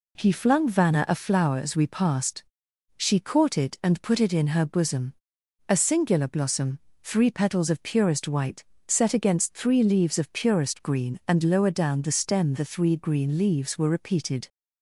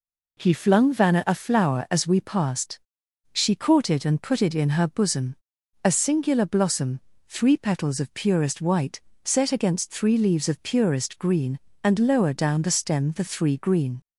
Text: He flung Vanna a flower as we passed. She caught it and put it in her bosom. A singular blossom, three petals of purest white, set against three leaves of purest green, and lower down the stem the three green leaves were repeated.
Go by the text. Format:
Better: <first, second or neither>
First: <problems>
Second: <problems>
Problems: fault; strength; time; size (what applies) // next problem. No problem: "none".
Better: first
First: none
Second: stops before "leaves were repeated"; at 14.0 s